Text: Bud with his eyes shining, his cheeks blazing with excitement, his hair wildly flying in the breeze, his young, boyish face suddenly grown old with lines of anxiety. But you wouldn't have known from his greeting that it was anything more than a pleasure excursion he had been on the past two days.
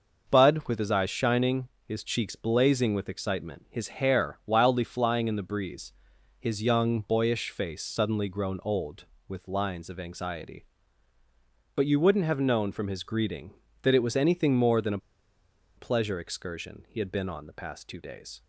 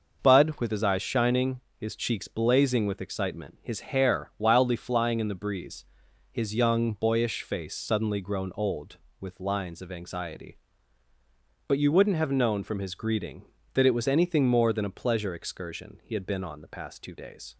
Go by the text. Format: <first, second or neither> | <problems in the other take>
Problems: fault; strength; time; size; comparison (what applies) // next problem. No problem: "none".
second | starts louder than the rest; noticeable; until 1.3 s; 6 dB; noticeable in the second // pauses between "a" and "pleasure"; noticeable; at 14.9 s; 0.79 s long